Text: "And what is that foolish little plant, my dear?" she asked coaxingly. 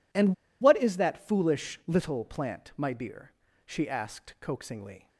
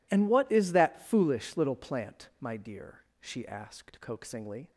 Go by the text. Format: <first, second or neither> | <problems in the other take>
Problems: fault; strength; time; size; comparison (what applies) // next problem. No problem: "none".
second | pauses between "And" and "what"; slight; at 0.3 s; 0.27 s long